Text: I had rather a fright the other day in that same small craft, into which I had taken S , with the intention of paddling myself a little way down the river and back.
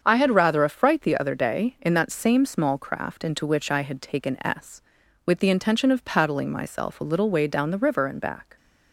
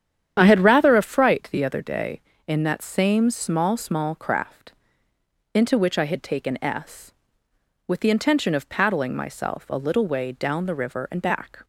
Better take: first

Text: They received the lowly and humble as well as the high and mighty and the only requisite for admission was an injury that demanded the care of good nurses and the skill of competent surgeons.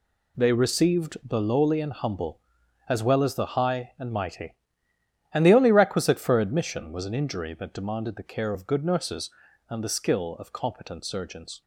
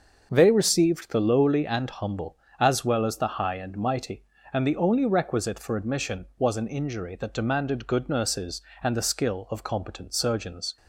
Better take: first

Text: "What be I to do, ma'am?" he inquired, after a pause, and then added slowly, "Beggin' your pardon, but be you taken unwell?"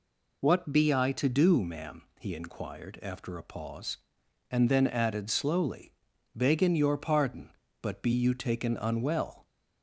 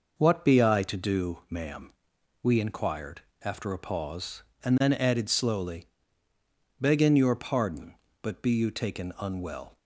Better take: first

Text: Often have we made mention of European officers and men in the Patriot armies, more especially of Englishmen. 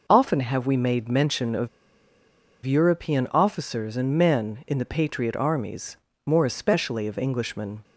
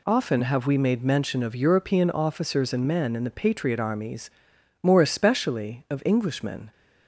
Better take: second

